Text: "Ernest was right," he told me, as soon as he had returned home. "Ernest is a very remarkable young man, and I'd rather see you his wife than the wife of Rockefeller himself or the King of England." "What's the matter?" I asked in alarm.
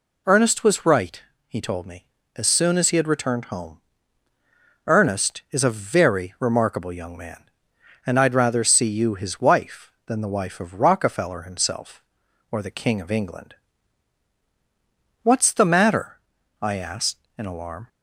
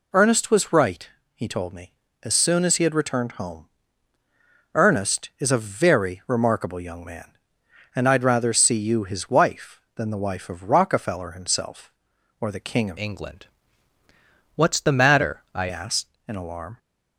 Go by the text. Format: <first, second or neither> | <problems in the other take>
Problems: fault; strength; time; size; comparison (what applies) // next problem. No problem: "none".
first | changes voice from "England" to "I"; from 12.9 to 15.6 s; 2.7 s long